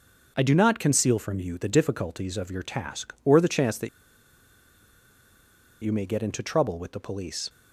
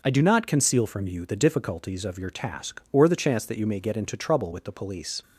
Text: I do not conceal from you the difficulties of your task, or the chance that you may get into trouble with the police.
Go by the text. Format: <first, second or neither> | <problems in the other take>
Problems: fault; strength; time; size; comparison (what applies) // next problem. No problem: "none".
second | pauses between "that" and "you"; strong; at 3.8 s; 1.9 s long